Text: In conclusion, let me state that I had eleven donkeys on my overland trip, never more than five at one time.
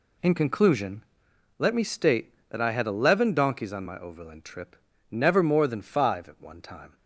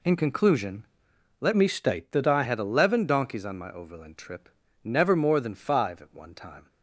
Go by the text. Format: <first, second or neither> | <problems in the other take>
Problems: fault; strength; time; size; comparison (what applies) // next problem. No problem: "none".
first | changes voice from "me" to "I"; from 1.5 to 2.4 s; 0.9 s long